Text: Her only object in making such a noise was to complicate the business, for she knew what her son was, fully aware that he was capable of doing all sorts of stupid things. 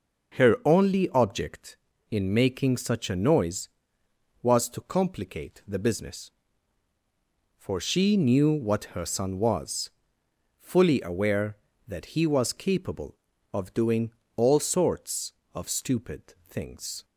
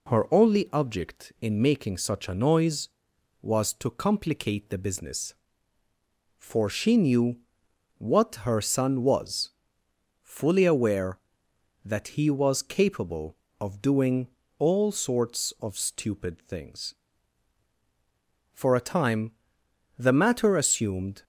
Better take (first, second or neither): first